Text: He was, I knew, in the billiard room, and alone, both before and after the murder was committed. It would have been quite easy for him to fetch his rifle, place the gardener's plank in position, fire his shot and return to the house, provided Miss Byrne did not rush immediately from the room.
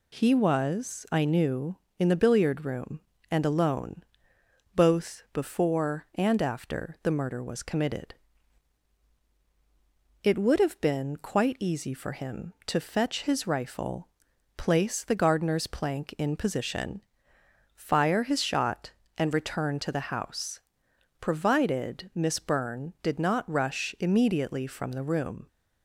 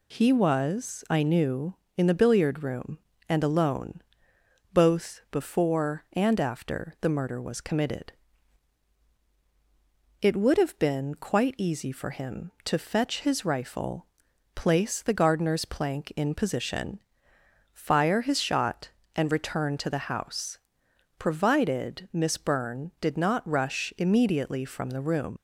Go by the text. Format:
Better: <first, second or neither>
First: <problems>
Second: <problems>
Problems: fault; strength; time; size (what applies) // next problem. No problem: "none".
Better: first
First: none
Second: leaves "room" unfinished; at 25.3 s; 85 ms